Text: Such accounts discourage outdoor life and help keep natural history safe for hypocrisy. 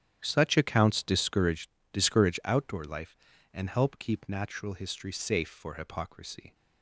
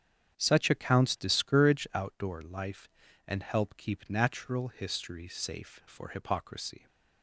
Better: second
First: starts louder than the rest; strong; until 1.2 s; 10.5 dB // says "discourage" twice; at 1.9 s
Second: starts louder than the rest; strong; until 1.4 s; 8.5 dB

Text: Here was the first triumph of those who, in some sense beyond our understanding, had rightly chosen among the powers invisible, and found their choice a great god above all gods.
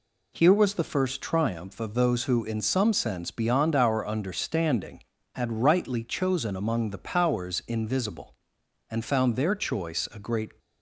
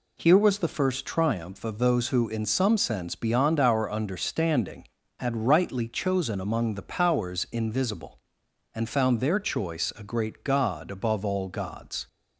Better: second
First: stops before "god above all gods"; at 10.5 s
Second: none

